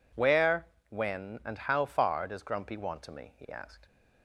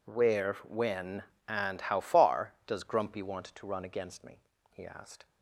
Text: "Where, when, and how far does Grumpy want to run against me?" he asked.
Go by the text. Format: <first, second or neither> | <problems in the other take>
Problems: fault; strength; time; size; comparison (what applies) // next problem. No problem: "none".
second | skips "run against"; at 3.1 s